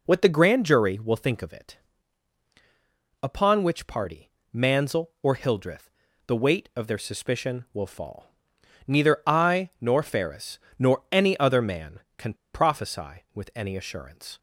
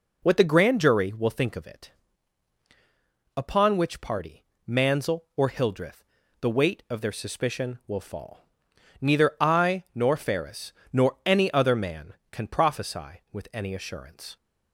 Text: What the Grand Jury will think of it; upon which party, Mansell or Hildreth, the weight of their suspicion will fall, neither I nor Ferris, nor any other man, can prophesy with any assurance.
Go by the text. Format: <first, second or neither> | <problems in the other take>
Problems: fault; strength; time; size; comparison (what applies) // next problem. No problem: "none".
second | pauses between "can" and "prophesy"; slight; at 12.3 s; 0.18 s long